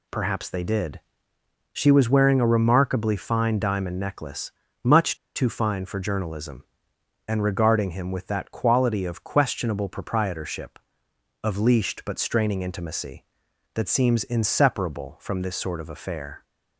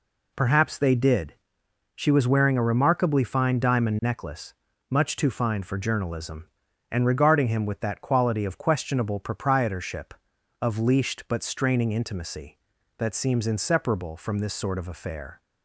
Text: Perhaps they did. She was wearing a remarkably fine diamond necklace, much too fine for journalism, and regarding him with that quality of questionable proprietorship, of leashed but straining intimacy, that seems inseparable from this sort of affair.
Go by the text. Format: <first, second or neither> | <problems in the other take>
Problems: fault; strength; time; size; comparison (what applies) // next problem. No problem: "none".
second | pauses between "much" and "too"; slight; at 5.1 s; 0.19 s long